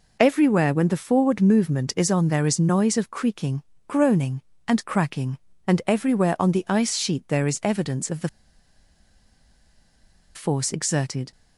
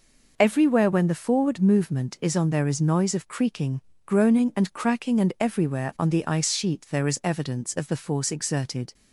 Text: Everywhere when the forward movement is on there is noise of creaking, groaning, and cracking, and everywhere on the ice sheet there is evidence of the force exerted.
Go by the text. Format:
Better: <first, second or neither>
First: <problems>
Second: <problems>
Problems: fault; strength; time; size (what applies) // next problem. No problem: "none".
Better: second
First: pauses between "the" and "force"; strong; at 8.2 s; 2.0 s long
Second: none